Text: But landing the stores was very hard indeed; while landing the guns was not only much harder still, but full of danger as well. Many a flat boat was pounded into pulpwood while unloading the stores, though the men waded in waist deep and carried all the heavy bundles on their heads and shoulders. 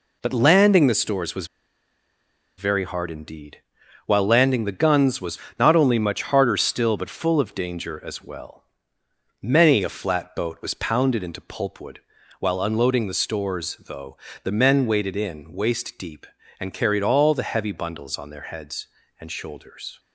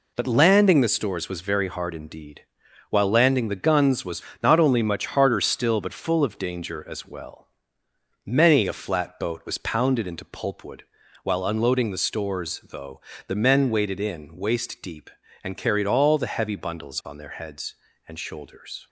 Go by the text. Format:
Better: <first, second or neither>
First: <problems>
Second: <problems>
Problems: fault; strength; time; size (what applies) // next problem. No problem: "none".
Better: second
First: pauses between "was" and "very"; at 1.4 s; 1.1 s long // pauses between "was" and "not"; slight; at 5.3 s; 0.22 s long // pauses between "pulpwood" and "while"; at 11.9 s; 0.40 s long // pauses between "though" and "the"; slight; at 14.1 s; 0.26 s long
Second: pauses between "was" and "not"; slight; at 4.2 s; 0.22 s long // pauses between "pulpwood" and "while"; at 10.8 s; 0.40 s long // pauses between "though" and "the"; slight; at 13.0 s; 0.26 s long